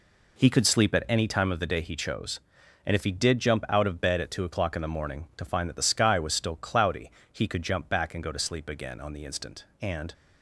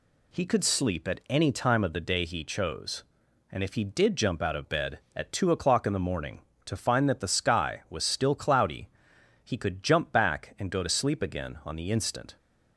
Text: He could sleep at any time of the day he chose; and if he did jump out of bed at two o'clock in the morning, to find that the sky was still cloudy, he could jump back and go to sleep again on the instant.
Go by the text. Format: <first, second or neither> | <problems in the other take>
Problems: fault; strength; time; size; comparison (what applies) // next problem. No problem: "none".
second | goes on to say "And"; slight; from 9.8 s on; 0.32 s long